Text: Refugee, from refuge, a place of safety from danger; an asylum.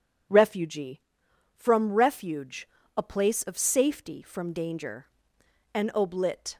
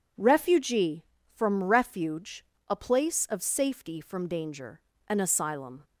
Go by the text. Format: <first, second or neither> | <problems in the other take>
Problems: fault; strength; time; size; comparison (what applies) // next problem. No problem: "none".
second | says "oblit" for "asylum"; at 5.9 s